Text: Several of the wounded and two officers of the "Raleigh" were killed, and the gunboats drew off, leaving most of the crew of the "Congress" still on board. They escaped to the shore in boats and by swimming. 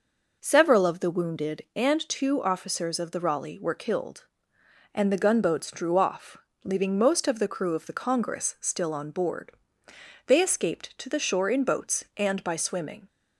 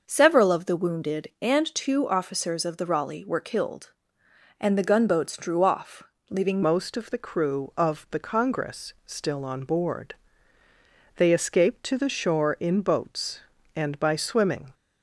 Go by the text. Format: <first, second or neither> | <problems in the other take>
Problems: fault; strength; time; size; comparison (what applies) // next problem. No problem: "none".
first | starts louder than the rest; noticeable; until 1.0 s; 6 dB // changes voice at "most"; from 6.6 s on; 8.1 s long